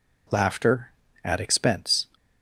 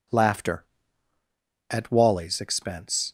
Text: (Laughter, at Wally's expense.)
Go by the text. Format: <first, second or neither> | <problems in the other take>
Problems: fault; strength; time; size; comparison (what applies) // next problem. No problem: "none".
second | skips "Wally's"; at 1.3 s